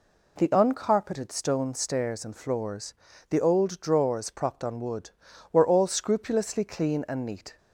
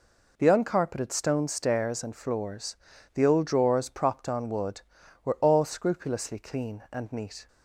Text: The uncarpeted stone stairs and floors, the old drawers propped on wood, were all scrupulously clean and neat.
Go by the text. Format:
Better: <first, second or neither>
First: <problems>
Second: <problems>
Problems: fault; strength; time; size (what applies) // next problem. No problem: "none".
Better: neither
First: none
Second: none